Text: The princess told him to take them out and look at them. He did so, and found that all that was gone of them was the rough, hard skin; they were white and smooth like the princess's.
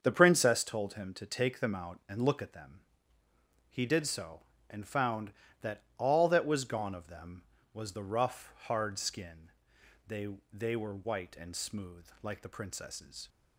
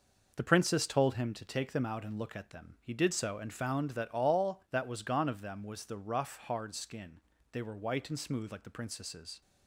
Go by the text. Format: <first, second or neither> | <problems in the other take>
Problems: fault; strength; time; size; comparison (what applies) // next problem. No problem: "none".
second | starts louder than the rest; until 1.0 s; 7 dB // says "they" twice; at 10.5 s // pauses between "smooth" and "like"; slight; at 12.0 s; 0.16 s long